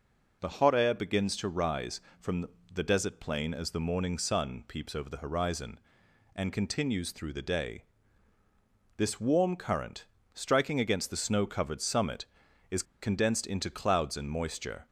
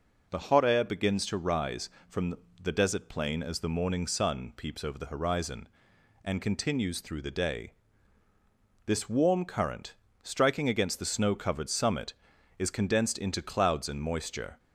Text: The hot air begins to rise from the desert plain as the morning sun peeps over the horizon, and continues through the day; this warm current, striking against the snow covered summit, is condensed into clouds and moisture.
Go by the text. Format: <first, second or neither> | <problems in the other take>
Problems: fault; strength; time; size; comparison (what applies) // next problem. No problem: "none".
second | pauses between "from" and "the"; slight; at 2.4 s; 0.26 s long; slight in the second // pauses between "is" and "condensed"; slight; at 12.8 s; 0.18 s long